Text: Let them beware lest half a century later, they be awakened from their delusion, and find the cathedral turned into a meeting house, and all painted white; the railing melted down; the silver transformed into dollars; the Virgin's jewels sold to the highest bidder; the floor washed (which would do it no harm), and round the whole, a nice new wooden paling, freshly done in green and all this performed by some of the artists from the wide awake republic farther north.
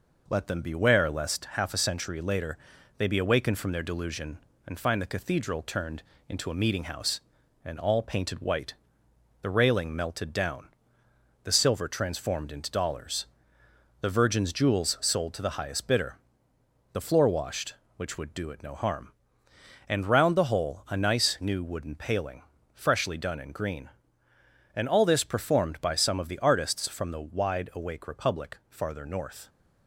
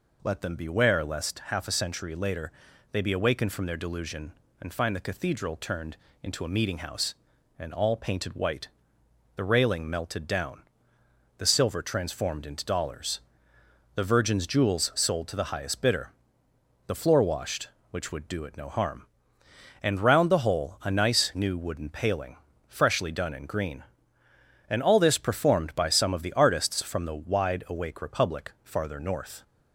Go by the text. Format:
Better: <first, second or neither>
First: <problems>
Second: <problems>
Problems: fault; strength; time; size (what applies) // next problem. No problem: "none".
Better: second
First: gets quieter; slight; throughout; 2.5 dB // pauses between "turned" and "into"; slight; at 6.0 s; 0.26 s long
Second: pauses between "turned" and "into"; slight; at 5.9 s; 0.26 s long